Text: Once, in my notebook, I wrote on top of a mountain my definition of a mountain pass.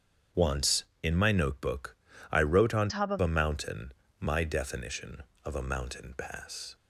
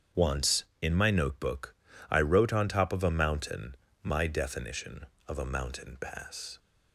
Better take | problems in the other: second | starts louder than the rest; strong; until 1.5 s; 8 dB; strong in the second // changes voice from "top" to "of"; from 2.8 to 3.1 s; 0.3 s long // pauses between "mountain" and "my"; slight; at 3.9 s; 0.26 s long; slight in the second

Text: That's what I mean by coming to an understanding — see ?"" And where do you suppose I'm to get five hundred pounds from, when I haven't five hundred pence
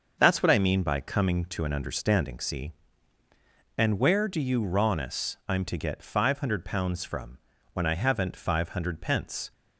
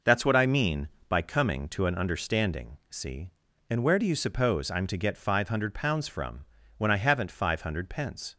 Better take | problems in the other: second | says "rawness" for "suppose"; at 4.6 s

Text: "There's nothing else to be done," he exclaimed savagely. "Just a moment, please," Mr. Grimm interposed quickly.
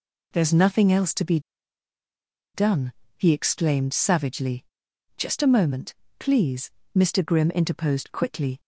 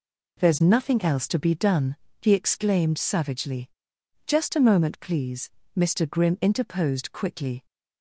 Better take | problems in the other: second | pauses between "be" and "done"; at 1.3 s; 1.1 s long

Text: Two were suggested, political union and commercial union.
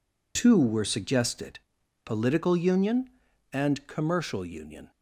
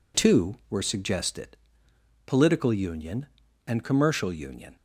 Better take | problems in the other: neither | none

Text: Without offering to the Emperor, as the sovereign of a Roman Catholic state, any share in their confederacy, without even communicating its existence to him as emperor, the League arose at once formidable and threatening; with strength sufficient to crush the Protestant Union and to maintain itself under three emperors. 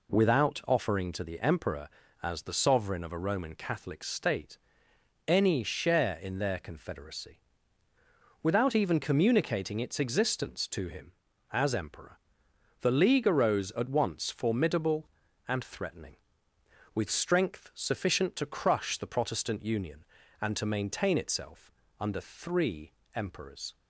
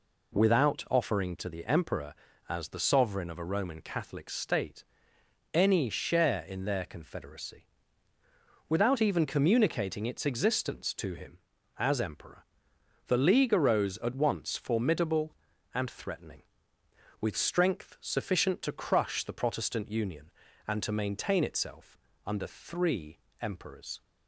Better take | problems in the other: neither | pauses between "itself" and "under"; slight; the same in both // pauses between "three" and "emperors"; slight; the same in both

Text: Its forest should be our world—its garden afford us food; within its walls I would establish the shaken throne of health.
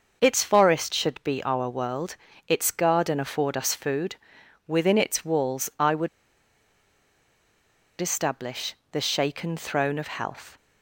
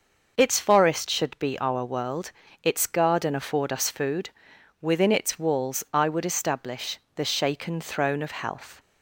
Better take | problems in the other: second | pauses between "would" and "establish"; strong; at 6.0 s; 1.9 s long // pauses between "establish" and "the"; slight; at 8.7 s; 0.16 s long; slight in the second

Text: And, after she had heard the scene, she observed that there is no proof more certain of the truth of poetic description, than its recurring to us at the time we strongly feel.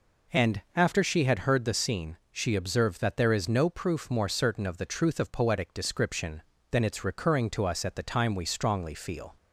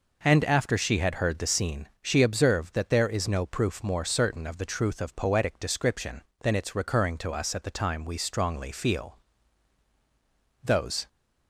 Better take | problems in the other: first | goes on to say "Those"; slight; from 10.6 s on; 0.44 s long

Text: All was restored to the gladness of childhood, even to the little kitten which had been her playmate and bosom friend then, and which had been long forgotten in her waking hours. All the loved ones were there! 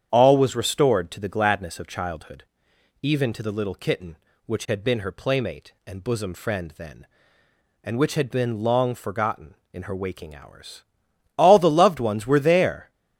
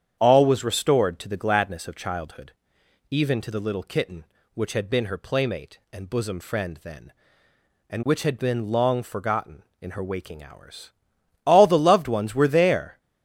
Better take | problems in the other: neither | starts louder than the rest; strong; the same in both

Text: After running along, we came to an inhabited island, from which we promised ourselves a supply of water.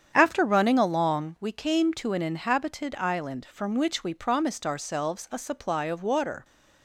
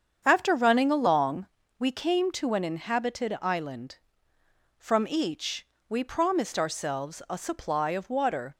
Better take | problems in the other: first | starts louder than the rest; strong; until 1.2 s; 7.5 dB; strong in the first // says "each" for "which"; at 5.0 s

